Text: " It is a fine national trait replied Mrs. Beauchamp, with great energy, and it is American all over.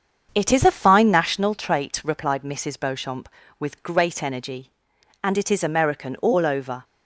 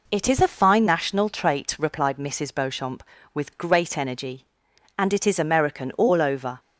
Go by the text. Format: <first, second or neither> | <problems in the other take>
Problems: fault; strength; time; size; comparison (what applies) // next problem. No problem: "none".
second | starts louder than the rest; strong; until 1.5 s; 7 dB